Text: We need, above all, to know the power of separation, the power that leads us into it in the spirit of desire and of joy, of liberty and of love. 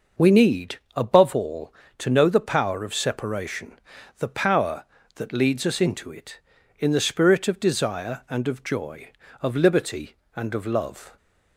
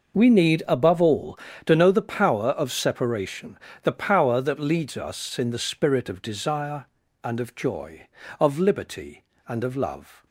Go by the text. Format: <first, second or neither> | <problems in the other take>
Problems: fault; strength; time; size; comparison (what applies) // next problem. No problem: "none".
first | skips "into it"; at 5.3 s